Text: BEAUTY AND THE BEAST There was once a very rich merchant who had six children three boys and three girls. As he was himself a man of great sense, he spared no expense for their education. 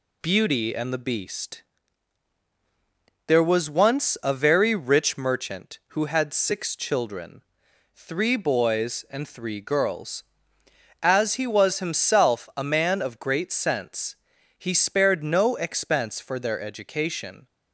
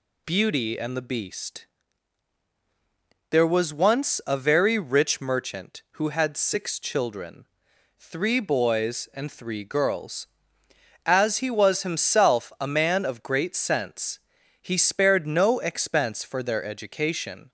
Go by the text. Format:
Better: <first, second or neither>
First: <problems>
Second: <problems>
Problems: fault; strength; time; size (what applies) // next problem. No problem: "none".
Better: second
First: gets quieter; slight; throughout; 2.5 dB // pauses between "BEAST" and "There"; strong; at 1.6 s; 1.6 s long // pauses between "children" and "three"; noticeable; at 7.4 s; 0.54 s long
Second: pauses between "BEAST" and "There"; strong; at 1.6 s; 1.6 s long // pauses between "children" and "three"; noticeable; at 7.4 s; 0.54 s long